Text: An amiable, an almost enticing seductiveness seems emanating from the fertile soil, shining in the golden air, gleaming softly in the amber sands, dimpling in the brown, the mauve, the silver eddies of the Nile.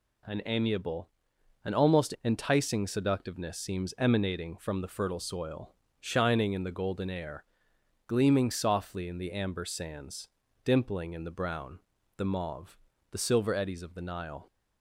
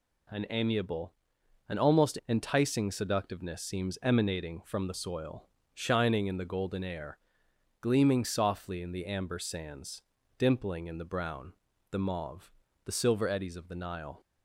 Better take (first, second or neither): first